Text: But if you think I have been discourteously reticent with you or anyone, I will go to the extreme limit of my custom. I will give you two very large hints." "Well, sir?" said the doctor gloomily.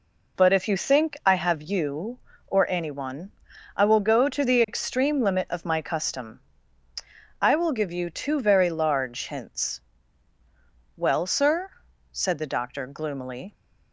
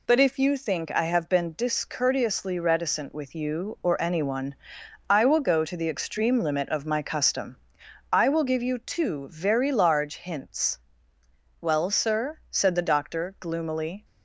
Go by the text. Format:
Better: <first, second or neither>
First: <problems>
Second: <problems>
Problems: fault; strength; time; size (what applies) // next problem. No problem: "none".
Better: second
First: skips "been discourteously reticent with"; at 1.6 s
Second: none